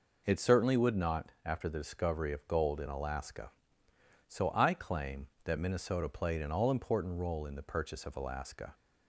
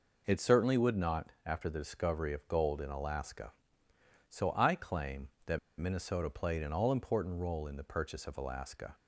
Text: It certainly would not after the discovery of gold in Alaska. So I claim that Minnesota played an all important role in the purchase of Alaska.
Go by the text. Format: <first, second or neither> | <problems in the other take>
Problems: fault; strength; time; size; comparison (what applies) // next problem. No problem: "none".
first | pauses between "that" and "Minnesota"; slight; at 5.5 s; 0.20 s long